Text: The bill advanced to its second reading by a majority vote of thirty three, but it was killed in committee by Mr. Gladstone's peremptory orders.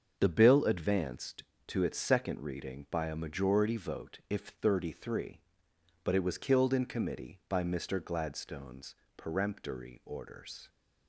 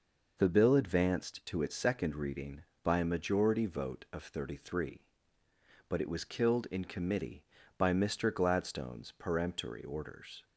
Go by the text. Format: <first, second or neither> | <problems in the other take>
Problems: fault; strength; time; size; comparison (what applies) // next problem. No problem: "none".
second | starts louder than the rest; until 1.1 s; 6.5 dB // says "if" for "of"; at 4.3 s // pauses between "Gladstone's" and "peremptory"; slight; at 8.9 s; 0.22 s long